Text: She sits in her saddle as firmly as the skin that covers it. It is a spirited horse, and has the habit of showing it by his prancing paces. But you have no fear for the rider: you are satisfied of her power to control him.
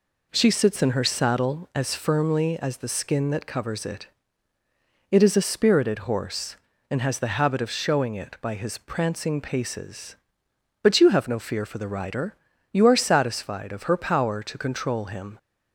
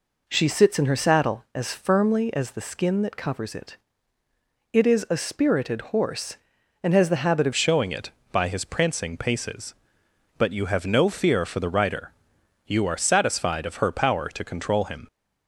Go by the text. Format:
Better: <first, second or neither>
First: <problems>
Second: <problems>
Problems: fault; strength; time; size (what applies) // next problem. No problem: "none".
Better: first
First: none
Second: changes voice at "showing"; from 7.5 s on; 7.5 s long